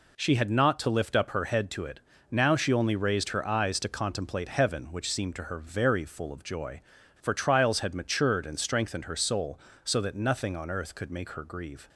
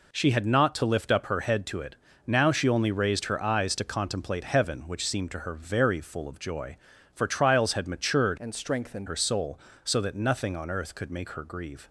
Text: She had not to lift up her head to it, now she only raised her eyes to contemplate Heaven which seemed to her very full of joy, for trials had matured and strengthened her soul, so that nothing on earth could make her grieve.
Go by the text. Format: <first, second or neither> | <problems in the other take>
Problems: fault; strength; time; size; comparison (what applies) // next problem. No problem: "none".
first | changes voice from "and" to "strengthened"; from 8.3 to 9.0 s; 0.7 s long